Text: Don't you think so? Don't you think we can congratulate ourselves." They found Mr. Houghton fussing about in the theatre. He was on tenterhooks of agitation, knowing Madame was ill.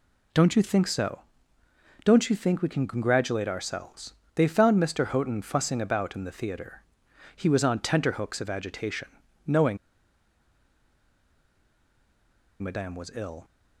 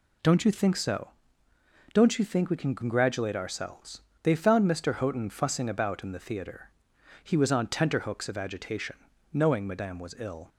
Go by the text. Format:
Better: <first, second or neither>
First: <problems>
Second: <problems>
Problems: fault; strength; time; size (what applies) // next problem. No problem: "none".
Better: second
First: pauses between "knowing" and "Madame"; strong; at 9.7 s; 2.8 s long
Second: none